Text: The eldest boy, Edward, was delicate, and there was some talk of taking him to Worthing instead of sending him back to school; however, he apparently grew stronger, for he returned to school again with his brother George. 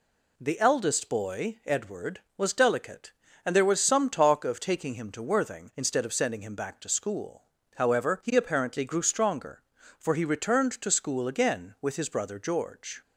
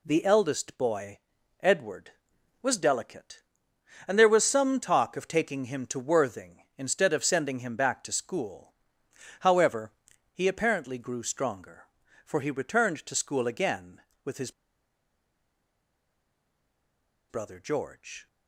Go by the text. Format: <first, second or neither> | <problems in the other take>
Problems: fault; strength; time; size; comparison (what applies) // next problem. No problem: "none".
first | pauses between "his" and "brother"; strong; at 14.4 s; 2.7 s long